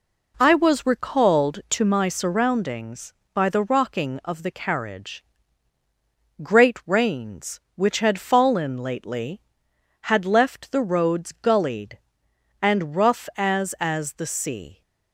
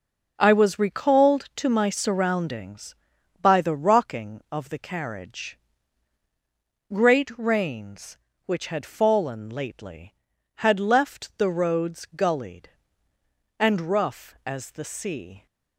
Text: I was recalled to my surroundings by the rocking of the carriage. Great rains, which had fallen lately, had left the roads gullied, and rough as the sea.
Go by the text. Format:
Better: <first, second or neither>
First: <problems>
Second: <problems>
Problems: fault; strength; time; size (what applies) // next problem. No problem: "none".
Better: second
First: says "as" twice; at 13.7 s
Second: none